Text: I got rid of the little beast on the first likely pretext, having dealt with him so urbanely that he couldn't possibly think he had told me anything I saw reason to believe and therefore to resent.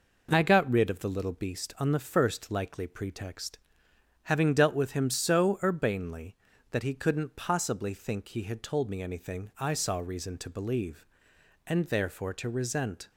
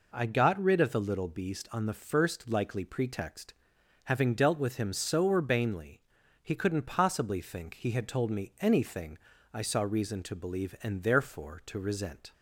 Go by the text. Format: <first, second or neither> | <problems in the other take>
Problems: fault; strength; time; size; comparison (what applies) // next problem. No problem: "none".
first | skips "that"; at 6.2 s // pauses between "anything" and "I"; at 9.1 s; 0.38 s long